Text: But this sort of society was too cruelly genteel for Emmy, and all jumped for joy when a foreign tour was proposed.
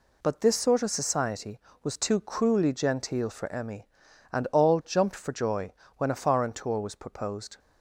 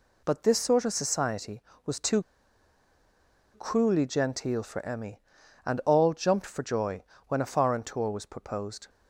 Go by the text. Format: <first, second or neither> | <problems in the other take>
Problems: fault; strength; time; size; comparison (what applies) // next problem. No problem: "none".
first | pauses between "too" and "cruelly"; strong; at 2.2 s; 1.3 s long // pauses between "joy" and "when"; slight; at 7.0 s; 0.26 s long; slight in the first